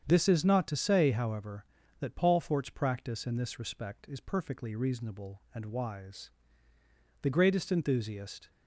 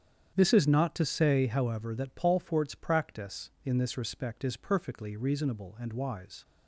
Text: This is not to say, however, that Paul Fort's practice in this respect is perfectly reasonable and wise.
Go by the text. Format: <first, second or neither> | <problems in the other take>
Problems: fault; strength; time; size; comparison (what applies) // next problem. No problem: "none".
second | starts louder than the rest; strong; until 1.0 s; 8 dB; strong in the second // goes on to say "The greatest enthusiast"; noticeable; from 7.2 s on; 1.2 s long